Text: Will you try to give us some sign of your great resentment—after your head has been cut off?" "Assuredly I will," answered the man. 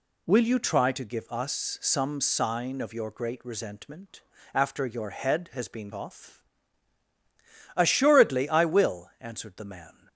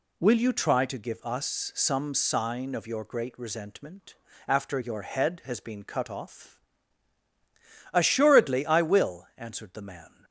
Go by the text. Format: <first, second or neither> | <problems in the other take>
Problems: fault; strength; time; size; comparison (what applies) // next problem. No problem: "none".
second | skips "cut"; at 5.9 s